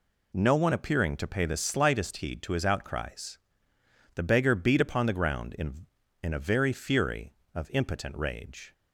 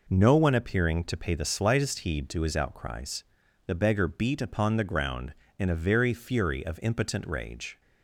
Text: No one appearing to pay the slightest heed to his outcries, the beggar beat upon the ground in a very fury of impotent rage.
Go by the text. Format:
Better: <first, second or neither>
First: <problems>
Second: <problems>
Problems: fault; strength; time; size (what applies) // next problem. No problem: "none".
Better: second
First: says "in" twice; at 6.2 s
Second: none